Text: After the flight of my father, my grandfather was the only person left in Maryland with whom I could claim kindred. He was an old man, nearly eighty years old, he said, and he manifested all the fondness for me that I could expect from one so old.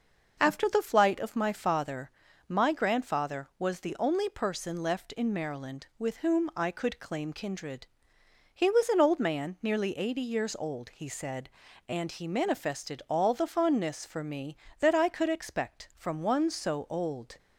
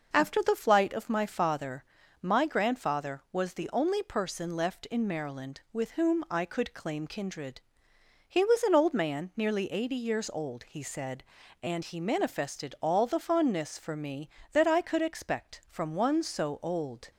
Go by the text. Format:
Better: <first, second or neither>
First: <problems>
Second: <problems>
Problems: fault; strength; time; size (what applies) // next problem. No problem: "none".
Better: neither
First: none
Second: none